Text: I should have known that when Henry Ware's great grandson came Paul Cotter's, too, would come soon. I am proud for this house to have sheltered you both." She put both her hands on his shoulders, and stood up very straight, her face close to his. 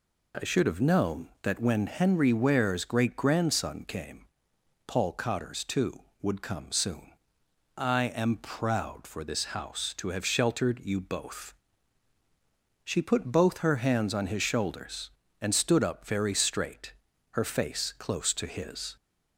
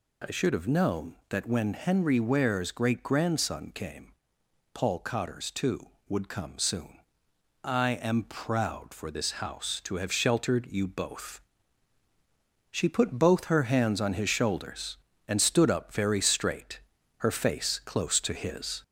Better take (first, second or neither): first